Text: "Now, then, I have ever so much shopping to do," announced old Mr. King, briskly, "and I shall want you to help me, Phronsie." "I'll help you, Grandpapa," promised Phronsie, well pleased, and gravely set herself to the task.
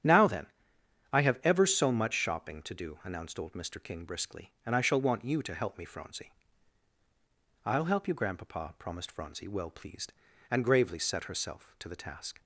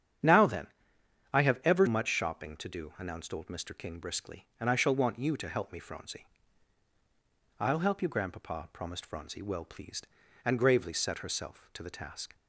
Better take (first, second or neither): first